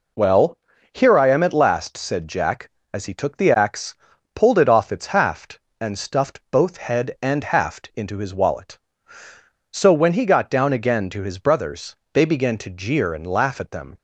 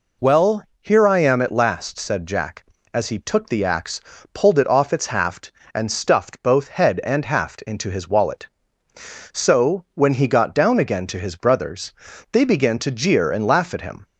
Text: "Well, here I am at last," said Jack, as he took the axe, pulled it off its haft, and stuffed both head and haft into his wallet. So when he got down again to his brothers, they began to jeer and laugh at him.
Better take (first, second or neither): second